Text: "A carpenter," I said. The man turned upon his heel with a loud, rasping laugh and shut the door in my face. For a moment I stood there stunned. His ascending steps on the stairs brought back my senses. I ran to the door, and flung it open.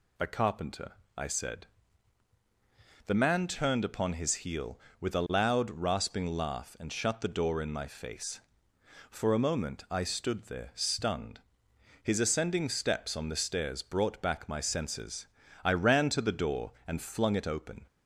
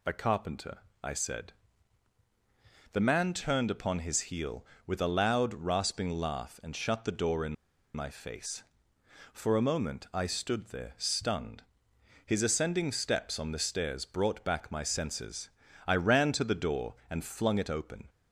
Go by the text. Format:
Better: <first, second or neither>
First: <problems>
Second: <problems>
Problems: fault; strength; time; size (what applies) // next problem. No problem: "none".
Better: first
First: none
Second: pauses between "in" and "my"; at 7.5 s; 0.40 s long